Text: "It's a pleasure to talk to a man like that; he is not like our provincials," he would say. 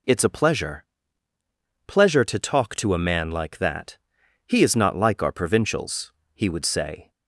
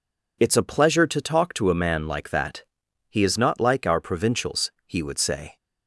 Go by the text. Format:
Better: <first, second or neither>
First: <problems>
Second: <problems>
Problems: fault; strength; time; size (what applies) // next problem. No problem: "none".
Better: second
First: says "pleasure" twice; at 1.8 s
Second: none